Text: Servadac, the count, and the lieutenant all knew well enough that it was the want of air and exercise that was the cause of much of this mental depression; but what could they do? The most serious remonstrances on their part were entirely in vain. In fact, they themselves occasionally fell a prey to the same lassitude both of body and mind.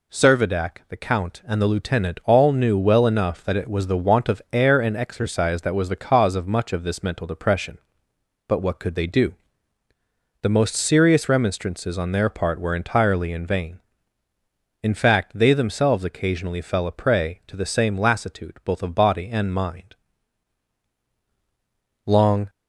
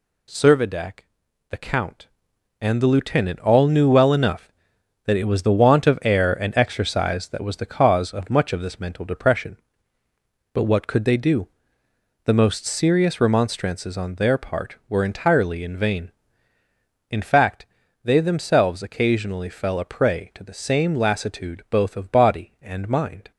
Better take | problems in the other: second | goes on to say "Long"; slight; from 22.0 s on; 0.42 s long

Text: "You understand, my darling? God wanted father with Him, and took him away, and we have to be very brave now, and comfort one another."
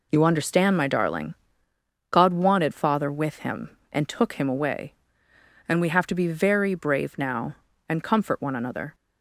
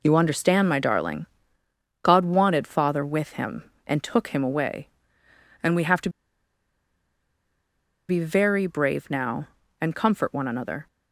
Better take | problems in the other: first | pauses between "to" and "be"; strong; at 6.0 s; 1.9 s long

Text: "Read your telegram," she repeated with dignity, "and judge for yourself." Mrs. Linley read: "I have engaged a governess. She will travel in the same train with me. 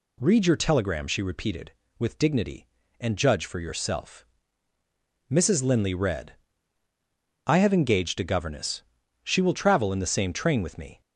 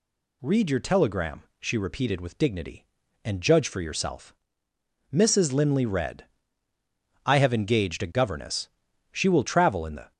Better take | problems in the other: first | stops before "same train with me"; at 10.1 s

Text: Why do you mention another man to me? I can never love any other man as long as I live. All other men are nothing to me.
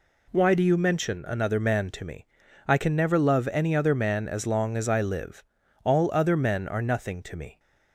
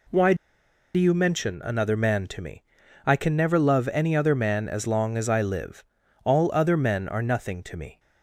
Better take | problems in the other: first | pauses between "do" and "you"; noticeable; at 0.3 s; 0.60 s long

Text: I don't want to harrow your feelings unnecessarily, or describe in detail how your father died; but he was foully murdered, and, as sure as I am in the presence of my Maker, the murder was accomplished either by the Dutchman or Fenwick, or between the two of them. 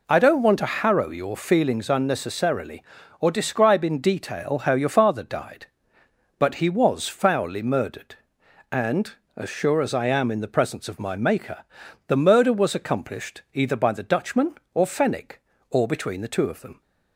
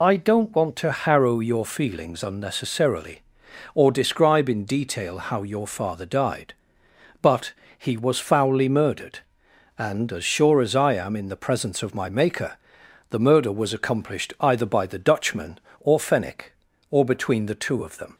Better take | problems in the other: first | loses the start of "I"; at 0.0 s; 35 ms // pauses between "but" and "he"; slight; at 7.5 s; 0.26 s long

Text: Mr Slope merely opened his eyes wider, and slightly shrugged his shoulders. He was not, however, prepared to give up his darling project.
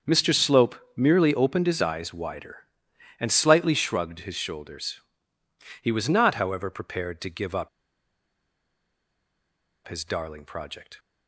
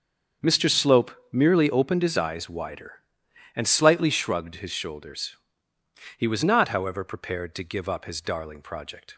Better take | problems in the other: second | starts louder than the rest; until 1.2 s; 7 dB; also in the second // pauses between "Slope" and "merely"; slight; at 0.7 s; 0.22 s long; slight in the second // pauses between "up" and "his"; strong; at 7.6 s; 2.1 s long

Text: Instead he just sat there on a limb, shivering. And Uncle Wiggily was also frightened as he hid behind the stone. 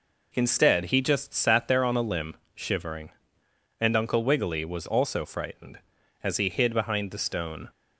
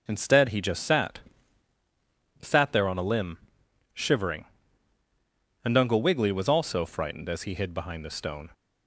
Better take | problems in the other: first | starts louder than the rest; until 1.0 s; 6.5 dB // says "sat" twice; at 2.4 s

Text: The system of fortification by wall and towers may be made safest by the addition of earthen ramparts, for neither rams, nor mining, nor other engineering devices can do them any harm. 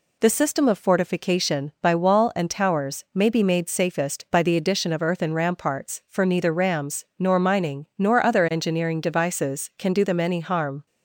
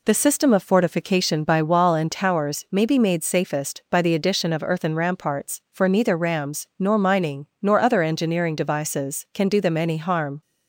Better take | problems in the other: neither | none

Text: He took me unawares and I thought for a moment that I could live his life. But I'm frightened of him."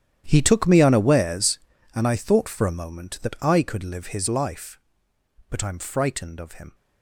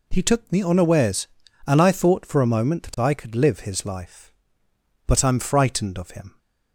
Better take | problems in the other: second | gets quieter; strong; throughout; 17.5 dB

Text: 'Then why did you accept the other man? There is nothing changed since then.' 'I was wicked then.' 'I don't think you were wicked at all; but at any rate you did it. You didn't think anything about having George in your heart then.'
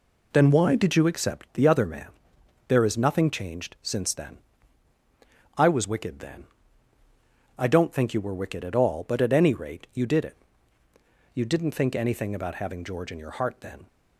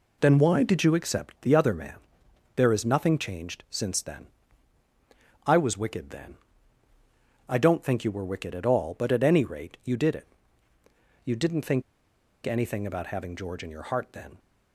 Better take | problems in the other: first | pauses between "think" and "anything"; noticeable; at 11.8 s; 0.62 s long

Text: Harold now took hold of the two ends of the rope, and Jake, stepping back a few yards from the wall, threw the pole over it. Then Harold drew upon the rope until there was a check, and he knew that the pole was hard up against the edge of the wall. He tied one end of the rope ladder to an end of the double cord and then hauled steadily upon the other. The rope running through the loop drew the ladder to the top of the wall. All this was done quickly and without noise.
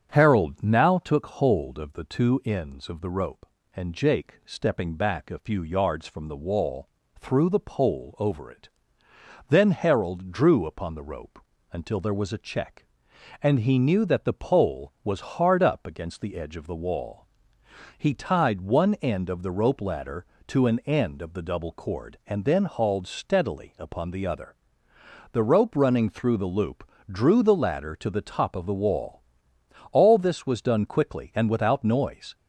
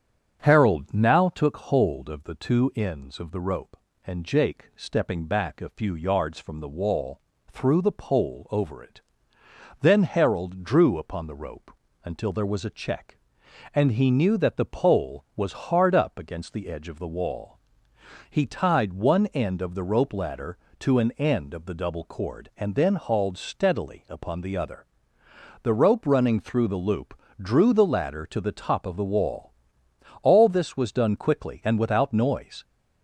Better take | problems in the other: neither | starts louder than the rest; strong; the same in both // pauses between "rope" and "until"; slight; the same in both // pauses between "loop" and "drew"; slight; the same in both

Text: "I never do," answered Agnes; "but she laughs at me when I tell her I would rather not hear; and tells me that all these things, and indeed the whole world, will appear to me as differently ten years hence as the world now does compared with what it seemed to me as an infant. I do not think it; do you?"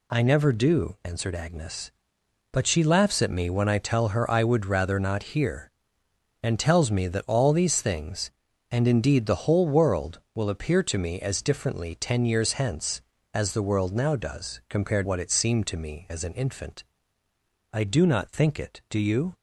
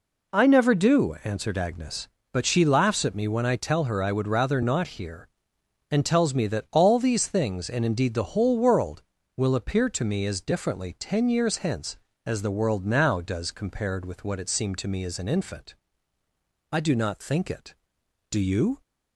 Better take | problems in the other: second | skips "with"; at 15.0 s

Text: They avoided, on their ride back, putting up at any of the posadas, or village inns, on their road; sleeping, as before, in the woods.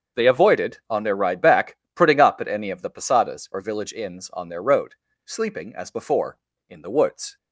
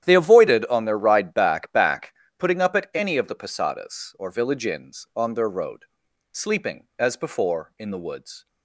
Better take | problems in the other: first | starts louder than the rest; strong; until 1.0 s; 10.5 dB; also in the first // says "back" twice; at 1.7 s

